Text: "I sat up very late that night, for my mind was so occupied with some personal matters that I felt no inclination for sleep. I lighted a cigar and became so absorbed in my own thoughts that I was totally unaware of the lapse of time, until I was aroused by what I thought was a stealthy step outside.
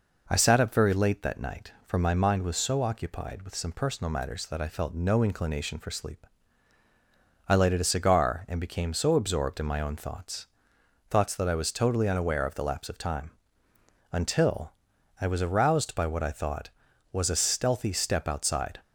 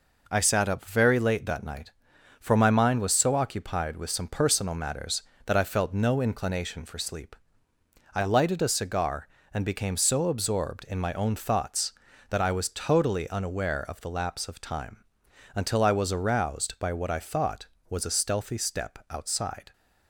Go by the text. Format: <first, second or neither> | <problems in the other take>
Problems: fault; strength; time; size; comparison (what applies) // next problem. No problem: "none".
second | says "thoughts" twice; at 11.0 s // pauses between "until" and "I"; noticeable; at 14.7 s; 0.48 s long